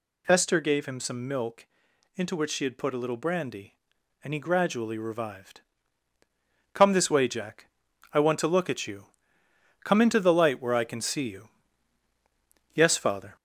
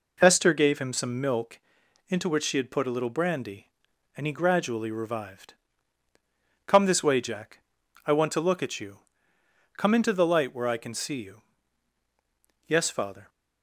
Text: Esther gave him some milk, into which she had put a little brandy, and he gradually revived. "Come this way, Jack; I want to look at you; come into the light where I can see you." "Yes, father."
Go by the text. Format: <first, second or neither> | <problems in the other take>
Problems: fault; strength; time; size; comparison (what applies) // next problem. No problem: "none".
second | gets louder; slight; throughout; 3.5 dB